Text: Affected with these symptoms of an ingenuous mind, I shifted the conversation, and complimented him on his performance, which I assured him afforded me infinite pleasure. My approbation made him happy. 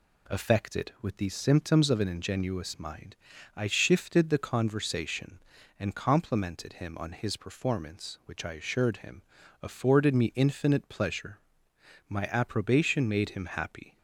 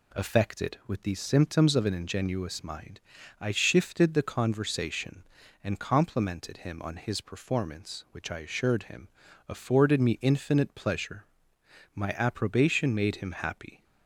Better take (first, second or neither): neither